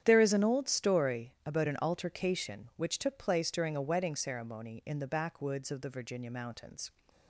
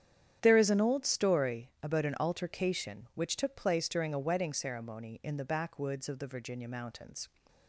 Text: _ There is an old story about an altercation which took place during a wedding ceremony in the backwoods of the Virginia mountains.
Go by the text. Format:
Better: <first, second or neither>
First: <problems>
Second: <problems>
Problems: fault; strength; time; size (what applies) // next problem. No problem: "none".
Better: neither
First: starts louder than the rest; strong; until 1.0 s; 9 dB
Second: starts louder than the rest; strong; until 1.4 s; 9 dB